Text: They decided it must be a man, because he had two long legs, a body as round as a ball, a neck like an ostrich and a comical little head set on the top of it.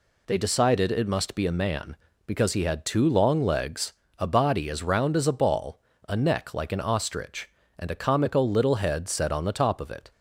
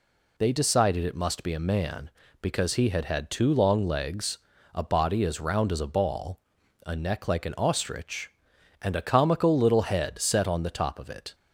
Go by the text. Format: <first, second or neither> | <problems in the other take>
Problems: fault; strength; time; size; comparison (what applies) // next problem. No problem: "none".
first | says "had" twice; at 3.0 s